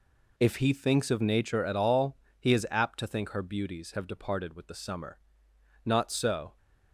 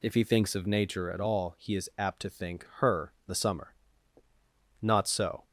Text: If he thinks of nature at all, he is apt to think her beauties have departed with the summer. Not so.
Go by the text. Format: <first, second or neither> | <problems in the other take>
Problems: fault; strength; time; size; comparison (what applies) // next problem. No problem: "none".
first | skips "beauties have departed with"; at 3.1 s